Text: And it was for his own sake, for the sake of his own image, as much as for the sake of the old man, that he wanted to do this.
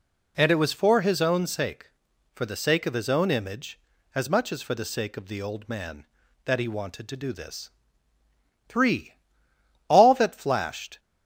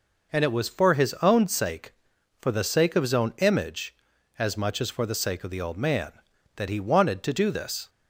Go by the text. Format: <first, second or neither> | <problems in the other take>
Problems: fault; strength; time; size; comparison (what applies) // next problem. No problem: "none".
second | goes on to say "THREE All that flashed"; strong; from 8.6 s on; 2.3 s long